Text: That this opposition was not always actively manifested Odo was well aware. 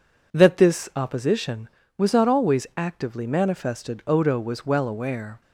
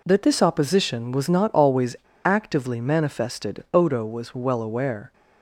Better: first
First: none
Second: pauses between "always" and "actively"; slight; at 1.9 s; 0.27 s long

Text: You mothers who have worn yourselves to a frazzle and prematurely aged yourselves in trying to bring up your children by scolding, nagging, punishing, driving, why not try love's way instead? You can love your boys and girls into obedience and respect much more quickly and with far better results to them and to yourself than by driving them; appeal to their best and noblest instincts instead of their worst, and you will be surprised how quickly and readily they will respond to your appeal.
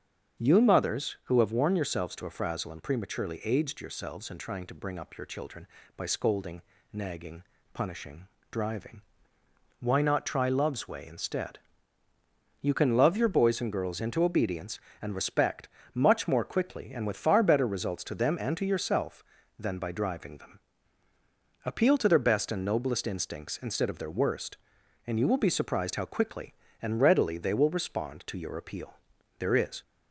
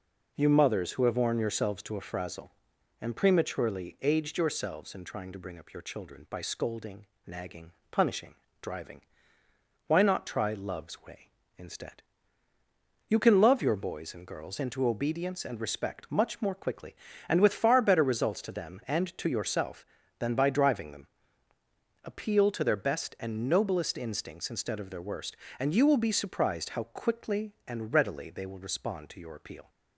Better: second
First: starts louder than the rest; strong; until 1.4 s; 7.5 dB // pauses between "respect" and "much"; slight; at 15.6 s; 0.28 s long // goes on to say "There is"; slight; from 29.3 s on; 0.42 s long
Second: none

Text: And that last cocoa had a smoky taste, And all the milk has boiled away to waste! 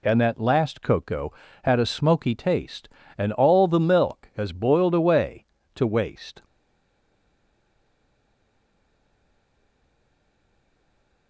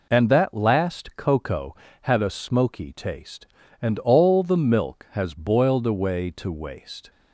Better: second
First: stays silent after the last word; strong; from 6.4 s on; 4.8 s long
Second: none

